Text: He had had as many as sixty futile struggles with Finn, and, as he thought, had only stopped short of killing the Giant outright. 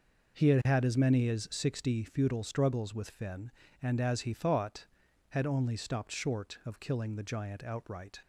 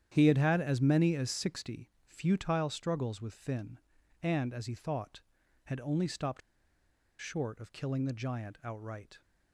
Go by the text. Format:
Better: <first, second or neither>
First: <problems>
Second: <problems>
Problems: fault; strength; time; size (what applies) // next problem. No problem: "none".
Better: first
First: none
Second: starts louder than the rest; strong; until 1.1 s; 10 dB // pauses between "stopped" and "short"; noticeable; at 6.4 s; 0.80 s long